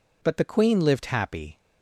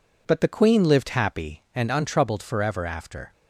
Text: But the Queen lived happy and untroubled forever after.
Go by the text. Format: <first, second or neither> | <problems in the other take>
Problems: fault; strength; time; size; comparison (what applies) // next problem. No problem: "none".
second | stops before "and untroubled forever after"; at 1.5 s